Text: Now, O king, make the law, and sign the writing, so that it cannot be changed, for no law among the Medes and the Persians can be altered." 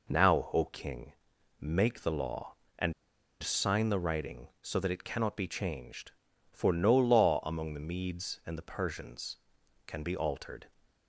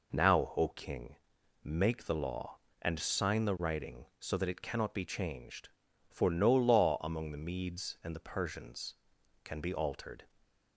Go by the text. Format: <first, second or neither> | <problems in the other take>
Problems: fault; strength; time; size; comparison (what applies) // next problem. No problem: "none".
second | pauses between "and" and "sign"; noticeable; at 2.9 s; 0.50 s long